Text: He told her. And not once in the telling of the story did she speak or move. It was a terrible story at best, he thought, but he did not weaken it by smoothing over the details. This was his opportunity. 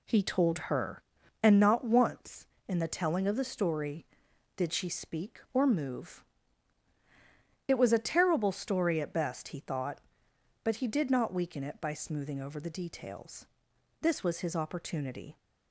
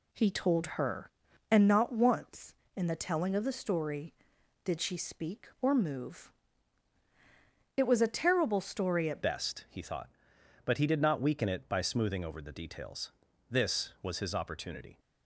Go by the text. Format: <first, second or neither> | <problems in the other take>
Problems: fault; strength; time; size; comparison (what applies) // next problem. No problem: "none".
first | changes voice at "best"; from 9.2 s on; 5.7 s long